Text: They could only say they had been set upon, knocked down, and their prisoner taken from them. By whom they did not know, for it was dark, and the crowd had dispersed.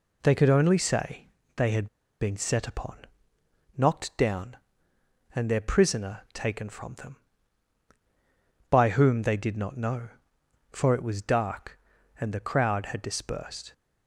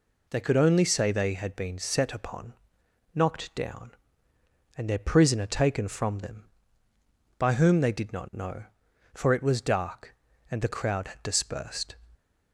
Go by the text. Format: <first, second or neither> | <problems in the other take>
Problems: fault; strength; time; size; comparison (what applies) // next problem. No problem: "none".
second | pauses between "say" and "they"; slight; at 1.2 s; 0.28 s long // pauses between "had" and "been"; slight; at 1.8 s; 0.34 s long